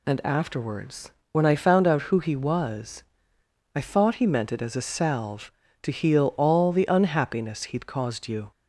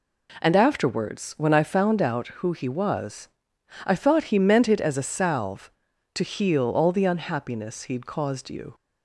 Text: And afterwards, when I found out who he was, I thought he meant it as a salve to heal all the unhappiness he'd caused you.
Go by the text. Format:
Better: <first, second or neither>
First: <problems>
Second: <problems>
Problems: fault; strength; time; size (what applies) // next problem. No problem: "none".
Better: neither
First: none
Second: none